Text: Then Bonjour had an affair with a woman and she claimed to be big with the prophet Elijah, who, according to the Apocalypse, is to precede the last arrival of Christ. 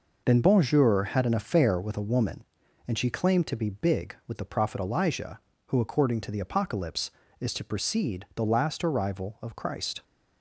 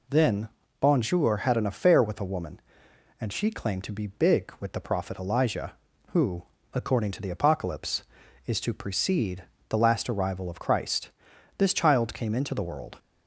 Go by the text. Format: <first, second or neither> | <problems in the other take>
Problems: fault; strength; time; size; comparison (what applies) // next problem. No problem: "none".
first | pauses between "Then" and "Bonjour"; slight; at 0.4 s; 0.30 s long // pauses between "precede" and "the"; slight; at 9.4 s; 0.26 s long // goes on to say "This child came into the world"; from 11.5 s on; 1.3 s long